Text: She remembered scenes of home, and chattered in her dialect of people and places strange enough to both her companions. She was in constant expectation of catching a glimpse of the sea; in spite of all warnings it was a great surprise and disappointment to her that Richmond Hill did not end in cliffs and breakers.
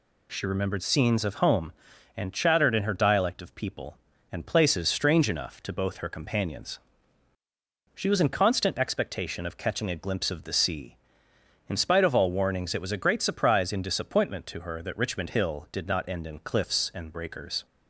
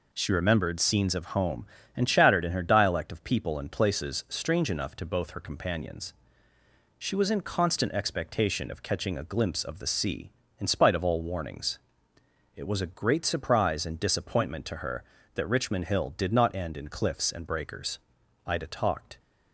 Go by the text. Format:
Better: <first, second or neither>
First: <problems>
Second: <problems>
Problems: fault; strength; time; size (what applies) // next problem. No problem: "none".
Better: first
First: none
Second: pauses between "warnings" and "it"; noticeable; at 11.7 s; 0.76 s long // goes on to say "Ida talked"; noticeable; from 18.4 s on; 0.72 s long